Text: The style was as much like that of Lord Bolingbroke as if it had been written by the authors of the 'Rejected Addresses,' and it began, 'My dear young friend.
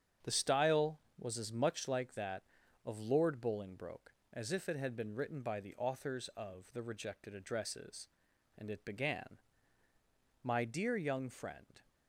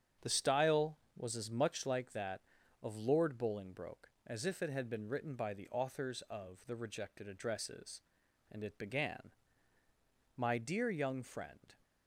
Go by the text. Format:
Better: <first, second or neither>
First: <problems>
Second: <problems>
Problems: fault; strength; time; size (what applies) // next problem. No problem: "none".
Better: neither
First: starts louder than the rest; strong; until 1.4 s; 8 dB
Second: starts louder than the rest; strong; until 1.3 s; 8 dB